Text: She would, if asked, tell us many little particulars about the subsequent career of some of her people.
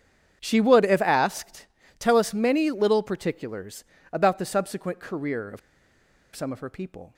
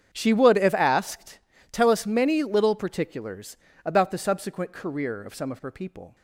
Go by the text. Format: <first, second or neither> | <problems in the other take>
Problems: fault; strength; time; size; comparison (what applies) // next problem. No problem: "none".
second | starts louder than the rest; strong; until 1.4 s; 8 dB; strong in the second // pauses between "particulars" and "about"; slight; at 3.8 s; 0.28 s long; slight in the second // pauses between "of" and "some"; noticeable; at 5.5 s; 0.75 s long